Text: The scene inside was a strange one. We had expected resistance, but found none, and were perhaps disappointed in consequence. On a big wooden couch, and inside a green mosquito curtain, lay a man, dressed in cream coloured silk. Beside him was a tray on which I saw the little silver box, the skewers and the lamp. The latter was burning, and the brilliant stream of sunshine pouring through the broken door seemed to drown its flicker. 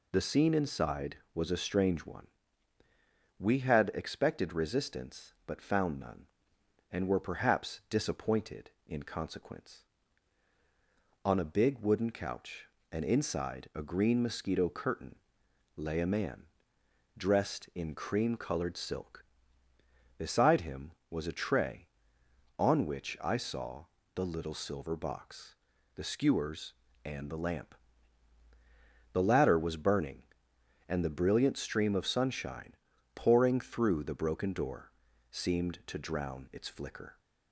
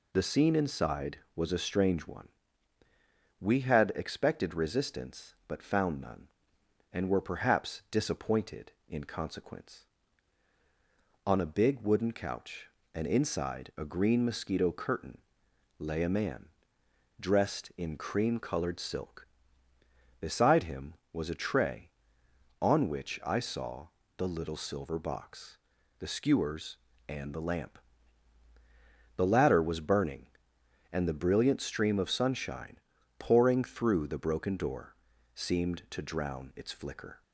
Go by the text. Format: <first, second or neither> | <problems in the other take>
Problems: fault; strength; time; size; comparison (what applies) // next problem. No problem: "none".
neither | pauses between "saw" and "the"; slight; the same in both // pauses between "sunshine" and "pouring"; the same in both // pauses between "door" and "seemed"; the same in both